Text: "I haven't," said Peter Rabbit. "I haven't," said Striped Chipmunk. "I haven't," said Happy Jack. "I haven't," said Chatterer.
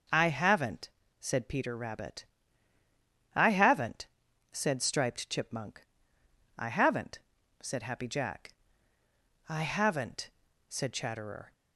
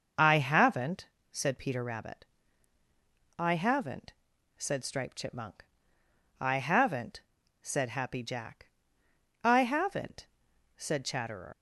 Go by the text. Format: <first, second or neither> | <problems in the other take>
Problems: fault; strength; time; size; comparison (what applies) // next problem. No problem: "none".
first | starts louder than the rest; noticeable; until 1.4 s; 6 dB // leaves "Chatterer" unfinished; at 11.5 s; 120 ms